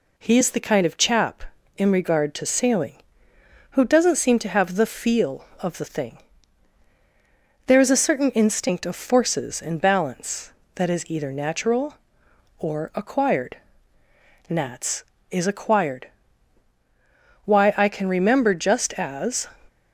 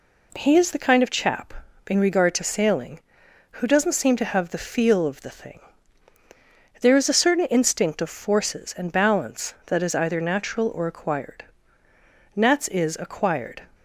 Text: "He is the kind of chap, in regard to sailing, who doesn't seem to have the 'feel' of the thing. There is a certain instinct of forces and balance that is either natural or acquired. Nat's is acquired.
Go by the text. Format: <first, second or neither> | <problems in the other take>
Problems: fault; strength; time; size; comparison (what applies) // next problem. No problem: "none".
second | goes on to say "Why I can remember just as"; strong; from 17.4 s on; 2.0 s long